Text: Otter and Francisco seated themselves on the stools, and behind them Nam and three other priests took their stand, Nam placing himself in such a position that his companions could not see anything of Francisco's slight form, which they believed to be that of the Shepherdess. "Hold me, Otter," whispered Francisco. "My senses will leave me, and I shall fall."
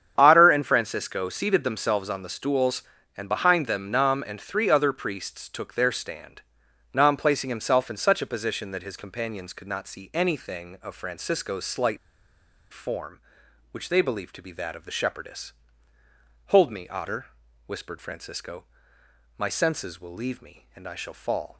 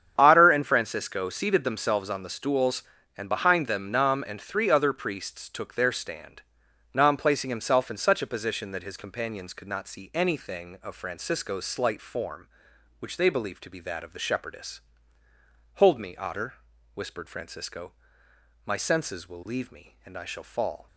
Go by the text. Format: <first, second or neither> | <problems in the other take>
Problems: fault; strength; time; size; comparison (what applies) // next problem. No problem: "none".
second | starts louder than the rest; strong; until 1.1 s; 8.5 dB; strong in the second // pauses between "slight" and "form"; noticeable; at 11.9 s; 0.74 s long